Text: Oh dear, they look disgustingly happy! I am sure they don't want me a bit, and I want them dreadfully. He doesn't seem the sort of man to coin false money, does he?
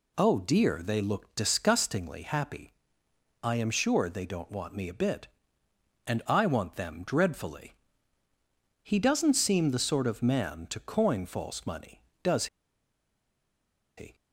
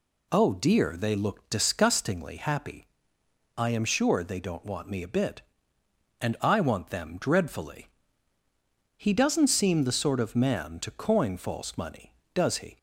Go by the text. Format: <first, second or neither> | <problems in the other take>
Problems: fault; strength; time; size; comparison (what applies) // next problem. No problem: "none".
second | pauses between "does" and "he"; strong; at 12.4 s; 1.5 s long